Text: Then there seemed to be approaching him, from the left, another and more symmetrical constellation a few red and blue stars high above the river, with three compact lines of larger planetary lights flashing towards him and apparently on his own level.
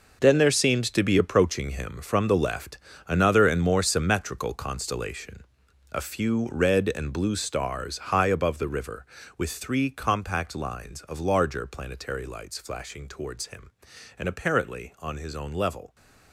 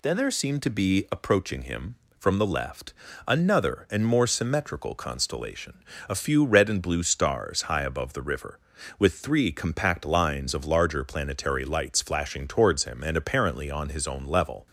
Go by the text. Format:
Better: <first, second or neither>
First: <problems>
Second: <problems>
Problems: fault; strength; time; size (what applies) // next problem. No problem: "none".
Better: second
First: gets quieter; strong; throughout; 13 dB // pauses between "constellation" and "a"; noticeable; at 5.4 s; 0.48 s long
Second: pauses between "constellation" and "a"; slight; at 5.8 s; 0.24 s long